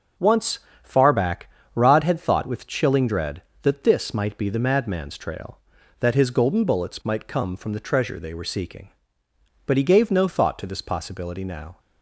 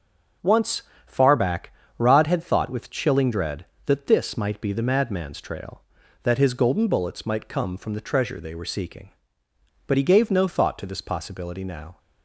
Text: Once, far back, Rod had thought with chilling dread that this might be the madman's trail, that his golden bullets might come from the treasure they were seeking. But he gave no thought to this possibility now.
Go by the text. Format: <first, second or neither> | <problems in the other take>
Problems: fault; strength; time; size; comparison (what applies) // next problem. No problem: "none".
neither | none